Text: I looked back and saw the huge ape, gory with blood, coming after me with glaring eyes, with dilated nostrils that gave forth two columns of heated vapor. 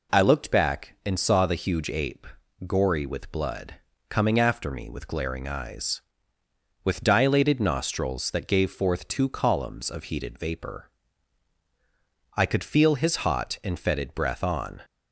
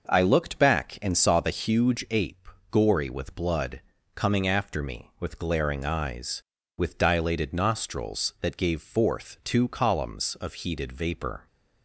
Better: second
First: goes on to say "I could feel his hot and fetid breath on"; strong; from 12.3 s on; 2.4 s long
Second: none

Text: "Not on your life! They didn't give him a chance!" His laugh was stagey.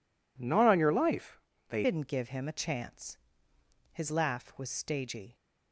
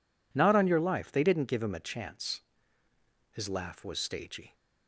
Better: second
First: changes voice at "didn't"; from 1.8 s on; 3.5 s long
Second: none

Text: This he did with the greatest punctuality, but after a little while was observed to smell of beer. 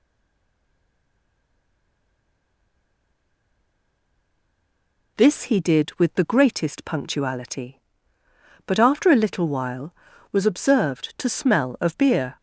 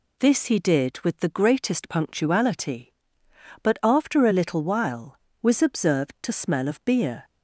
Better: second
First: stays silent before the first word; strong; until 5.1 s; 5.1 s long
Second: none

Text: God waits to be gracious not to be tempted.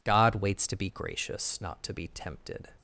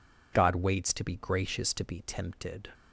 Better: first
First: none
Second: skips "not"; at 1.7 s

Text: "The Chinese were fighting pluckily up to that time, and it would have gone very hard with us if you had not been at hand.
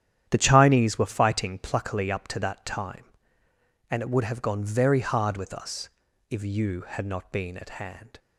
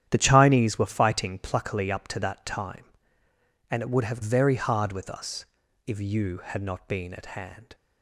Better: first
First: starts louder than the rest; strong; until 1.3 s; 10.5 dB // pauses between "us" and "if"; at 5.8 s; 0.42 s long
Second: starts louder than the rest; strong; until 1.1 s; 10.5 dB // skips "gone"; at 4.2 s // pauses between "us" and "if"; at 5.4 s; 0.42 s long

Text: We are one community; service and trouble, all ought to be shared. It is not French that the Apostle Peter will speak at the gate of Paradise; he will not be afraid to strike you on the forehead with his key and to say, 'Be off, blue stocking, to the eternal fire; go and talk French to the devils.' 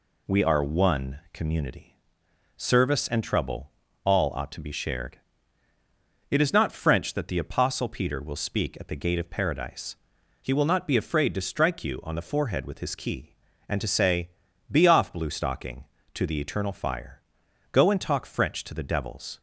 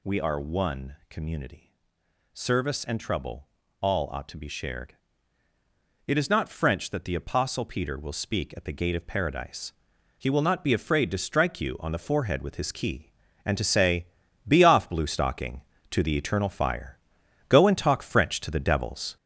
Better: first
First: pauses between "one" and "community"; slight; at 1.1 s; 0.16 s long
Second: gets louder; noticeable; throughout; 5.5 dB // pauses between "one" and "community"; slight; at 0.9 s; 0.16 s long

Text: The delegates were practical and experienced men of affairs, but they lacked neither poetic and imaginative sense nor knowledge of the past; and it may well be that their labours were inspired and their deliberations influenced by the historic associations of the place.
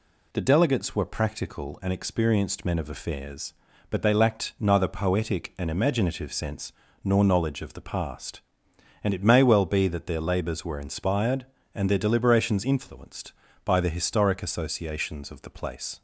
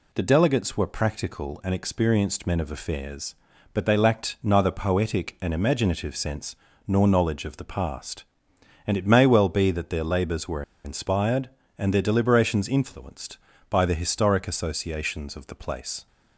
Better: first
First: pauses between "sense" and "nor"; slight; at 6.7 s; 0.32 s long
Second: pauses between "sense" and "nor"; slight; at 6.5 s; 0.32 s long // pauses between "were" and "inspired"; slight; at 10.6 s; 0.22 s long

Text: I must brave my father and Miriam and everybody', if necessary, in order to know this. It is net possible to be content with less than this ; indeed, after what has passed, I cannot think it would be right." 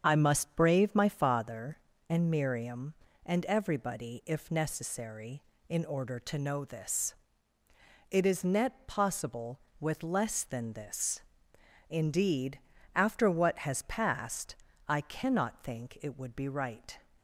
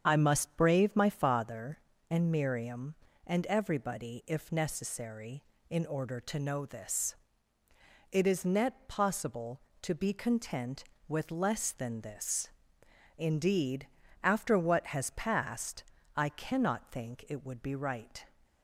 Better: second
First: starts louder than the rest; strong; until 1.0 s; 7.5 dB // skips "to be content"; at 9.6 s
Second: starts louder than the rest; strong; until 1.0 s; 7.5 dB

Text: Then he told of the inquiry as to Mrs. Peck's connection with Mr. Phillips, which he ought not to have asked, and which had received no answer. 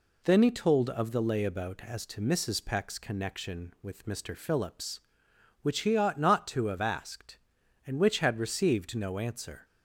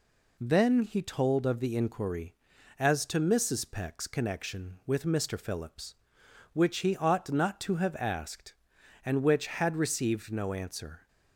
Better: second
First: says "layabout" for "inquiry"; at 1.2 s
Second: none

